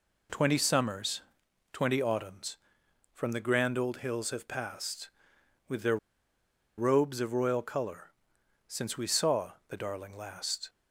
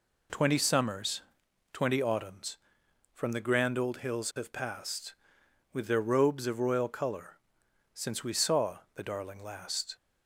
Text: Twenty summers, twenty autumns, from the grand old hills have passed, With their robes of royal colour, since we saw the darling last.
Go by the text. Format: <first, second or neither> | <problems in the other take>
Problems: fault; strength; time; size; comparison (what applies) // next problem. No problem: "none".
second | pauses between "their" and "robes"; noticeable; at 5.9 s; 0.81 s long // pauses between "saw" and "the"; slight; at 9.5 s; 0.16 s long; slight in the second